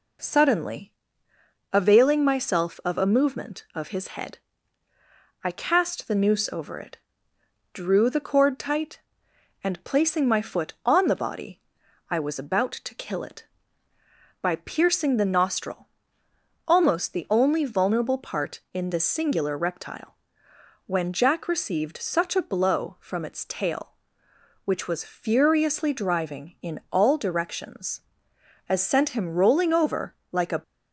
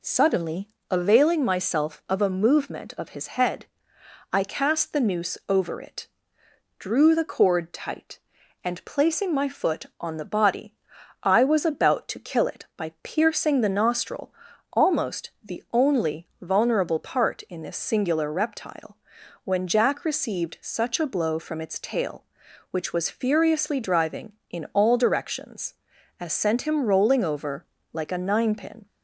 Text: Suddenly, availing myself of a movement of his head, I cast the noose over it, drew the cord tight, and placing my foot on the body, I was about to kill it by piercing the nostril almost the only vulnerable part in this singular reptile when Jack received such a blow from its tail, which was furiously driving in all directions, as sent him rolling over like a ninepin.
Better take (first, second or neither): second